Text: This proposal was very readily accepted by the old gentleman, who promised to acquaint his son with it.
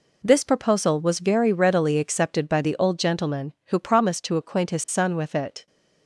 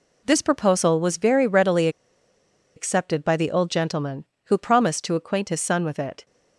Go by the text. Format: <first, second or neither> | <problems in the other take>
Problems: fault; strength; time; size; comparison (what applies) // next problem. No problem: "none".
first | pauses between "readily" and "accepted"; noticeable; at 1.8 s; 0.87 s long